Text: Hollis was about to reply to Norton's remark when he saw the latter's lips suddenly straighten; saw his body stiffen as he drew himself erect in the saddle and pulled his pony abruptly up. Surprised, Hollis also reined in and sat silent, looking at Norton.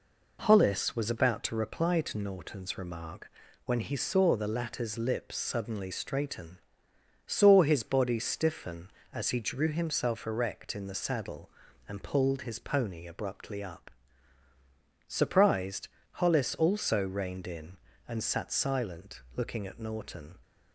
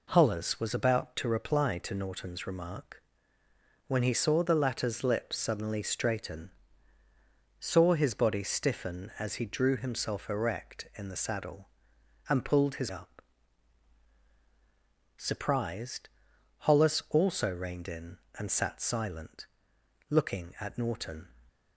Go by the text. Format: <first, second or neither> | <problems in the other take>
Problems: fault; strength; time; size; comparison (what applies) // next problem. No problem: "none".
first | pauses between "remark" and "when"; noticeable; at 3.0 s; 0.86 s long; slight in the first // skips "pony abruptly"; at 12.8 s